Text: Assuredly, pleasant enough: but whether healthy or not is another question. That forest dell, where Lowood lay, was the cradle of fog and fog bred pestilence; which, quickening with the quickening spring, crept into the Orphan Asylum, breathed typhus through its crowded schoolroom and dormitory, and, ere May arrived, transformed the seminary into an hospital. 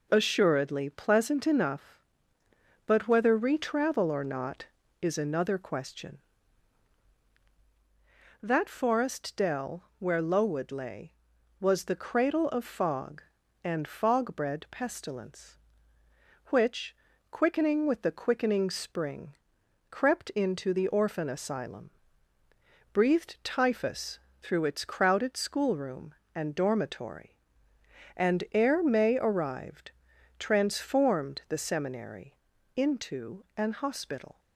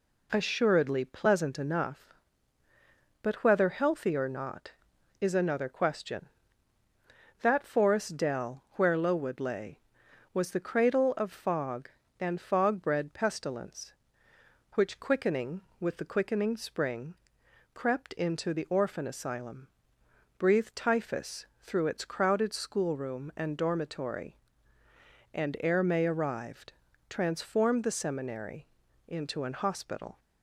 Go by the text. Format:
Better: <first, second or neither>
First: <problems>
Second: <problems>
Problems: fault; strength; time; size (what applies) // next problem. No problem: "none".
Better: second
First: says "retravel" for "healthy"; at 3.3 s // pauses between "typhus" and "through"; slight; at 24.1 s; 0.24 s long // pauses between "seminary" and "into"; at 32.3 s; 0.44 s long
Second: pauses between "seminary" and "into"; at 28.6 s; 0.40 s long